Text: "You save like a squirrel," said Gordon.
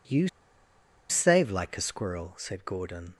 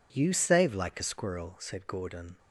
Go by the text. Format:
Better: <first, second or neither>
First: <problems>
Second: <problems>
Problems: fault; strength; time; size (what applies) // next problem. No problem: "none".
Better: second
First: pauses between "You" and "save"; noticeable; at 0.2 s; 0.81 s long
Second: none